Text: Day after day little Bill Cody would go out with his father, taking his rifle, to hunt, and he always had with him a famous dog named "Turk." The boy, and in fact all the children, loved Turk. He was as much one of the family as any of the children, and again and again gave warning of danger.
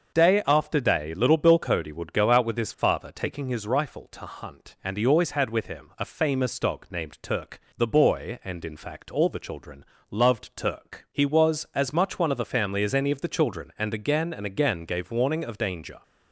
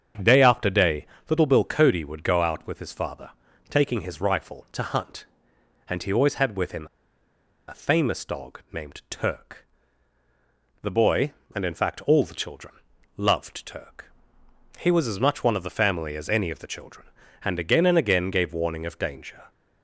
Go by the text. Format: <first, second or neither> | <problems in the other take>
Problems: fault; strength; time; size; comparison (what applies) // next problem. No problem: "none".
first | starts louder than the rest; strong; until 1.4 s; 7.5 dB; also in the first // pauses between "day" and "little"; slight; at 1.0 s; 0.22 s long // pauses between "him" and "a"; noticeable; at 6.8 s; 0.81 s long